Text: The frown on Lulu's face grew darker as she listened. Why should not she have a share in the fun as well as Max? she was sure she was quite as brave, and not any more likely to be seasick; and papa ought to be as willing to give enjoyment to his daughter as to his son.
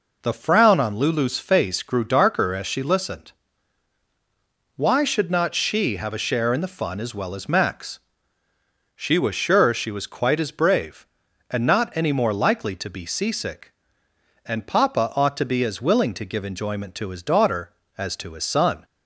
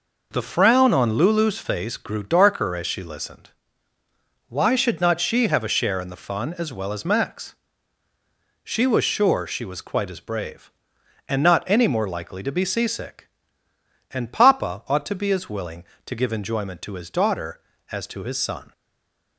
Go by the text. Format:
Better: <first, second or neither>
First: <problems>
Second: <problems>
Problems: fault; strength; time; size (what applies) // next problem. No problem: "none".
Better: first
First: none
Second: stays silent after the last word; slight; from 18.7 s on; 0.6 s long